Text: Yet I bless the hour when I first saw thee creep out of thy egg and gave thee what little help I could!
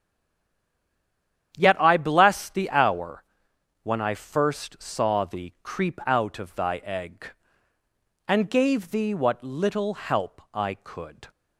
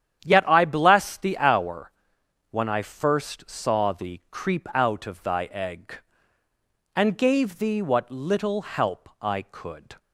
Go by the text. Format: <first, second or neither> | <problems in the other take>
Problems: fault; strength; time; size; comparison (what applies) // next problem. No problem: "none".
second | stays silent before the first word; noticeable; until 1.5 s; 1.5 s long // starts louder than the rest; strong; until 2.6 s; 9.5 dB; strong in the second // pauses between "hour" and "when"; noticeable; at 3.2 s; 0.60 s long; noticeable in the second